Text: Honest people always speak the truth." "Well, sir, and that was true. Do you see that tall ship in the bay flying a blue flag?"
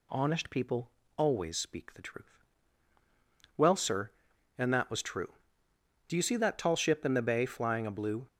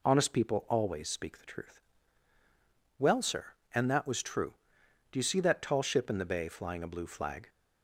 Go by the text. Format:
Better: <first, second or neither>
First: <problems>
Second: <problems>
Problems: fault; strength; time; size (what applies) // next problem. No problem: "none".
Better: second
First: pauses between "people" and "always"; slight; at 0.8 s; 0.26 s long // stops before "flag"; at 8.2 s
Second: none